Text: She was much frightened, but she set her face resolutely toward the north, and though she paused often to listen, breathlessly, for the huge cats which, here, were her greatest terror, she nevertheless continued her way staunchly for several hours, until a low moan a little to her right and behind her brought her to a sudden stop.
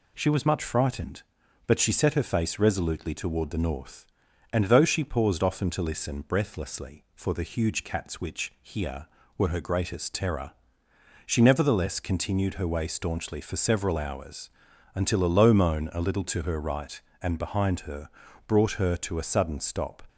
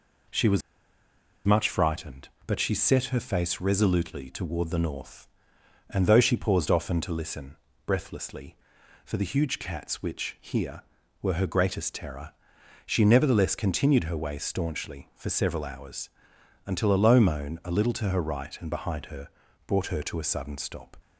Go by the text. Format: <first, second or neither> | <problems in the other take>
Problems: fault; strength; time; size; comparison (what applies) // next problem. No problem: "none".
first | pauses between "was" and "much"; noticeable; at 0.6 s; 0.85 s long // pauses between "her" and "brought"; at 19.2 s; 0.38 s long; slight in the first